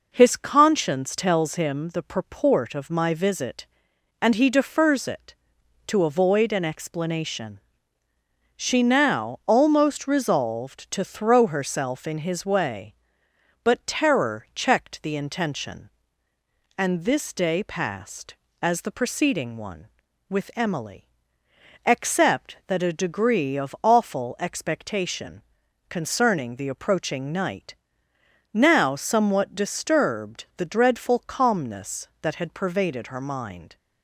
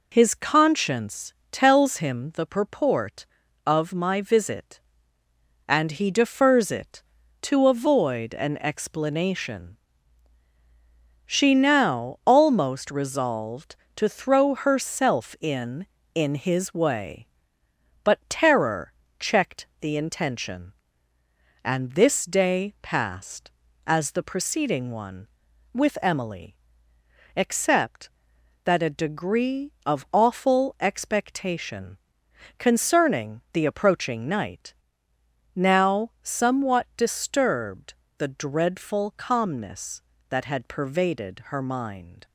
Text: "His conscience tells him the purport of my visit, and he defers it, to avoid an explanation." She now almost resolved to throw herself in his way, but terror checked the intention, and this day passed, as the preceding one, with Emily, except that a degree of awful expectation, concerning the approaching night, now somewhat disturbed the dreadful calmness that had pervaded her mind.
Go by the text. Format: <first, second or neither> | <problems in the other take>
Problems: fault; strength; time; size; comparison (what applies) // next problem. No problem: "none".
first | pauses between "conscience" and "tells"; slight; at 1.3 s; 0.18 s long // says "in" twice; at 16.1 s // pauses between "terror" and "checked"; slight; at 18.9 s; 0.26 s long // pauses between "checked" and "the"; slight; at 19.6 s; 0.16 s long // pauses between "disturbed" and "the"; slight; at 37.9 s; 0.26 s long